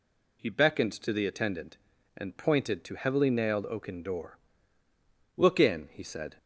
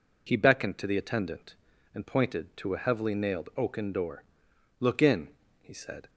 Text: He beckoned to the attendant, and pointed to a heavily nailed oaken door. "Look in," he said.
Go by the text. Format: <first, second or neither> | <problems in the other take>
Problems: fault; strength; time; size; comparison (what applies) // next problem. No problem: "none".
second | skips "a"; at 2.9 s